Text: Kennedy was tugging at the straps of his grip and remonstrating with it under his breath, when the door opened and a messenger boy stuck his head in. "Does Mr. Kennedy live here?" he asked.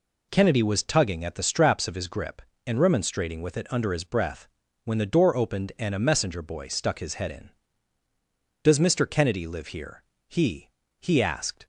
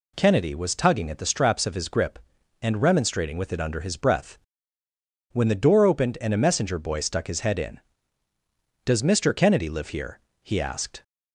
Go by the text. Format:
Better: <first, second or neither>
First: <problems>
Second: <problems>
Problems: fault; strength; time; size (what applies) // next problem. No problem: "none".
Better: second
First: says "he" twice; at 10.9 s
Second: none